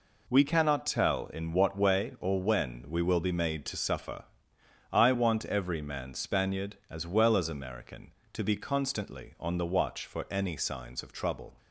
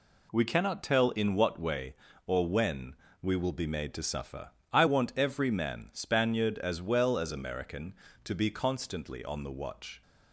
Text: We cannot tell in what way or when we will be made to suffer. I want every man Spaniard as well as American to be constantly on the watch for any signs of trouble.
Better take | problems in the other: first | pauses between "when" and "we"; slight; at 2.9 s; 0.26 s long // stops before "for any signs of trouble"; at 10.0 s

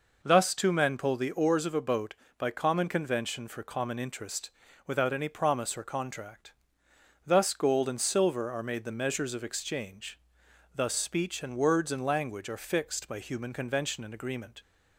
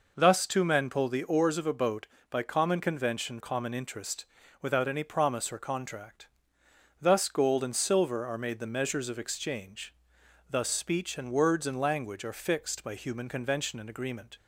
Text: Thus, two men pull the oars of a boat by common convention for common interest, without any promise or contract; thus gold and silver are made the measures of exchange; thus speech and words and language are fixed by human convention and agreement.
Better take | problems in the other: first | skips "for"; at 3.3 s

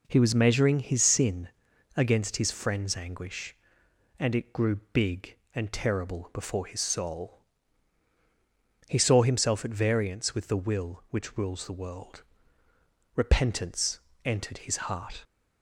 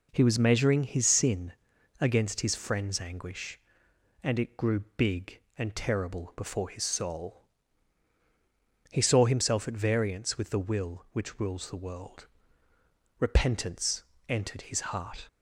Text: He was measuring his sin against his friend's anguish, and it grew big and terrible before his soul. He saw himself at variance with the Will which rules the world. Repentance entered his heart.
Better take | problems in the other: neither | pauses between "sin" and "against"; noticeable; the same in both // pauses between "grew" and "big"; slight; the same in both // pauses between "Repentance" and "entered"; slight; the same in both

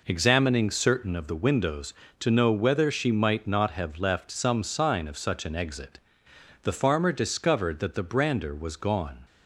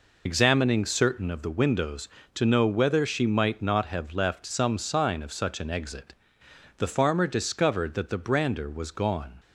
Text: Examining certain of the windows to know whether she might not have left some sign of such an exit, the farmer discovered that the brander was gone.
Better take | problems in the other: first | loses the start of "Examining"; at 0.2 s; 55 ms

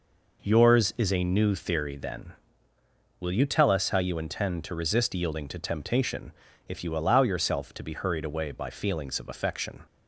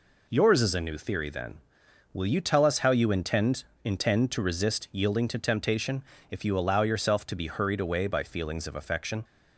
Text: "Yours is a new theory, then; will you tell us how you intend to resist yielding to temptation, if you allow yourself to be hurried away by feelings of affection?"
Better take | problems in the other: first | says "intend" twice; at 3.8 s

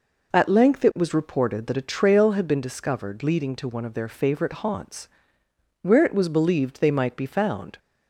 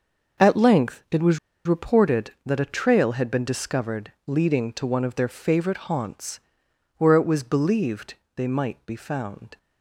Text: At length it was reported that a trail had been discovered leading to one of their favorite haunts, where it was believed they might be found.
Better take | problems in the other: first | starts louder than the rest; until 1.7 s; 6 dB // pauses between "was" and "reported"; slight; at 1.3 s; 0.28 s long // pauses between "believed" and "they"; slight; at 8.1 s; 0.20 s long

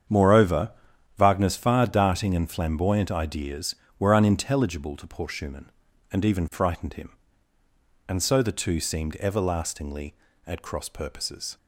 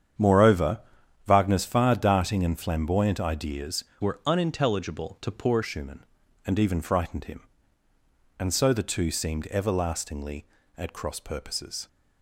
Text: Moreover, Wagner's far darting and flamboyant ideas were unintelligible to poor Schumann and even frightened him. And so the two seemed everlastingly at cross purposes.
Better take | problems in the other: first | starts louder than the rest; strong; until 1.6 s; 8.5 dB; strong in the first // changes voice from "were" to "poor"; from 4.0 to 5.6 s; 1.6 s long

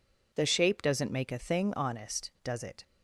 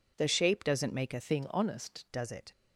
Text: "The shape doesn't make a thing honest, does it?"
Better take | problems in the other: first | changes voice from "thing" to "honest"; from 1.1 to 2.0 s; 0.9 s long

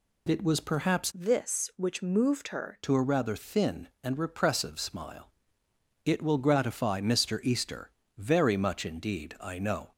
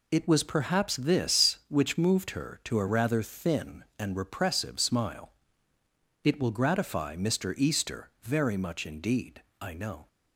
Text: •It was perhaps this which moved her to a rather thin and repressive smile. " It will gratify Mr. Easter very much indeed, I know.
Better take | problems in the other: second | changes voice from "this" to "her"; from 1.1 to 2.8 s; 1.7 s long // pauses between "Easter" and "very"; slight; at 7.9 s; 0.26 s long

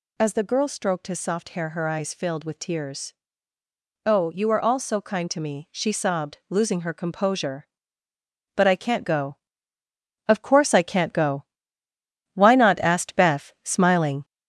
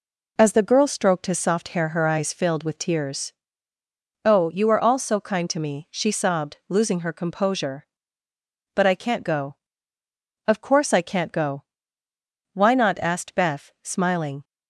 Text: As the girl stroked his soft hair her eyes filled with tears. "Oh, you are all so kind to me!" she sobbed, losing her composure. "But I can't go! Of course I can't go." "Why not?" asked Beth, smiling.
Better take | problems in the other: second | gets louder; noticeable; throughout; 4.5 dB

